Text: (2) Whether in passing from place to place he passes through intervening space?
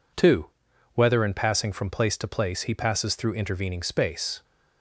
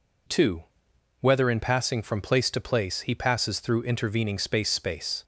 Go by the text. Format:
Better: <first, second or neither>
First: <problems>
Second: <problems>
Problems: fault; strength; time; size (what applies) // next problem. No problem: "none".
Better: first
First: none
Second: says "space" twice; at 4.6 s